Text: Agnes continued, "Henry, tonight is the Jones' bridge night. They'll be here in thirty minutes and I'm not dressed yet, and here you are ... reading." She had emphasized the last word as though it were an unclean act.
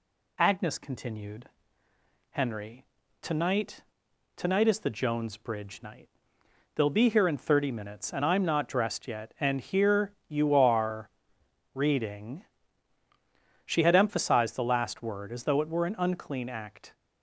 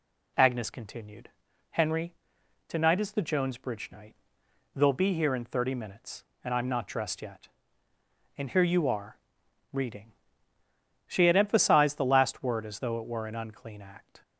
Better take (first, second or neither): second